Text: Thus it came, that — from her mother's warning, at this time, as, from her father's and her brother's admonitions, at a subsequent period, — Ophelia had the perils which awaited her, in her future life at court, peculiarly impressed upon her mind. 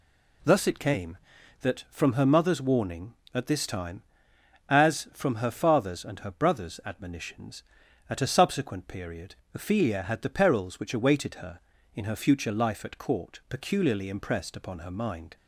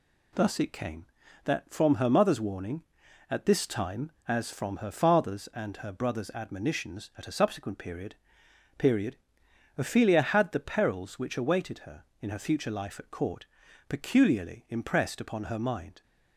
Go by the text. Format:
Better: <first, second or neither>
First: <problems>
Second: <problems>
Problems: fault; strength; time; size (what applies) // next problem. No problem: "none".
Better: first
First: none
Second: says "period" twice; at 8.7 s